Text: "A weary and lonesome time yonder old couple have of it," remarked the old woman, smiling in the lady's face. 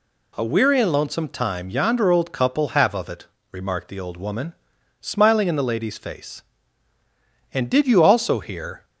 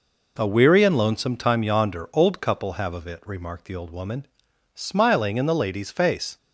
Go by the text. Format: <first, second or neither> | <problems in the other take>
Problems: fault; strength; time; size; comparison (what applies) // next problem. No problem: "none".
second | goes on to say "And did you also hear"; from 7.5 s on; 1.3 s long